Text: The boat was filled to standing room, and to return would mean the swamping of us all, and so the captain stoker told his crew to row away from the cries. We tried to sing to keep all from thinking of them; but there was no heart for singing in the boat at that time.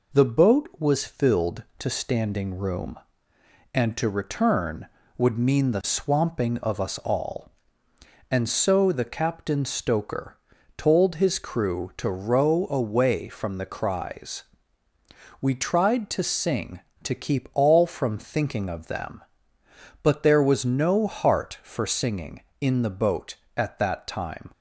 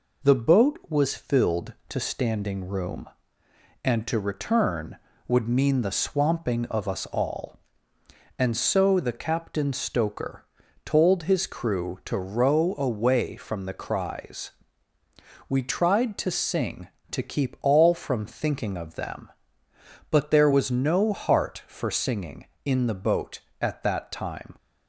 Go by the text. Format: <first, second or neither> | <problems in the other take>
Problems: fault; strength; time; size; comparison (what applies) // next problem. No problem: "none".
neither | pauses between "stoker" and "told"; the same in both